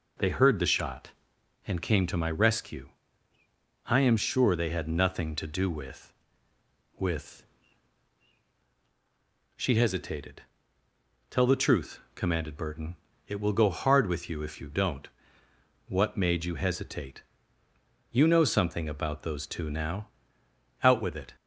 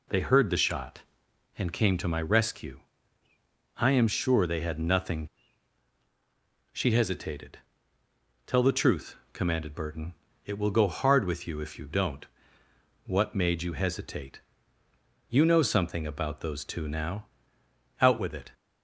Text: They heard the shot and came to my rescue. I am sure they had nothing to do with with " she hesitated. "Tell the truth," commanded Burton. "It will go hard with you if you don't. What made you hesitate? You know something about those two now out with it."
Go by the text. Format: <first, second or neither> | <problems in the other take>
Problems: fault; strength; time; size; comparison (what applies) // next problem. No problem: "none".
first | skips "to do with with"; at 5.4 s // pauses between "now" and "out"; noticeable; at 17.2 s; 0.74 s long; noticeable in the first